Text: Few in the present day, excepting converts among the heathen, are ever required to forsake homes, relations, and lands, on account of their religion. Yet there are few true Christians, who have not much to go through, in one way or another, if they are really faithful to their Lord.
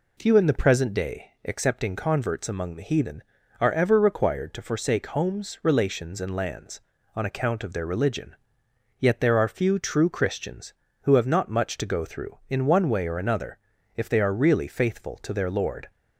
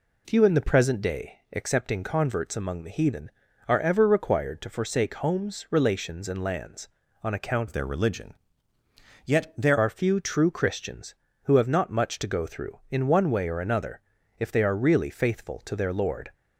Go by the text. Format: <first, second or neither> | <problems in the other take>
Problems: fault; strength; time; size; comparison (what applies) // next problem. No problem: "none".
first | changes voice from "of" to "there"; from 7.6 to 9.7 s; 2.1 s long